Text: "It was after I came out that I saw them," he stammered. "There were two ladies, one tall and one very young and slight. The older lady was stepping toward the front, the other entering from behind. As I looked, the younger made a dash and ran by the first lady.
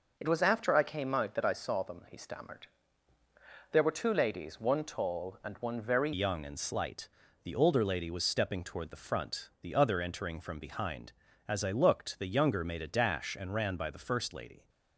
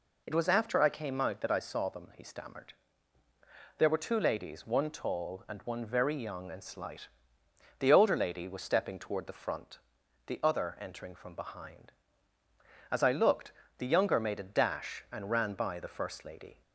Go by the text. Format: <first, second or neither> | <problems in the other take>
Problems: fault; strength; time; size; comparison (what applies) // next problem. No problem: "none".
second | changes voice at "young"; from 6.1 s on; 8.5 s long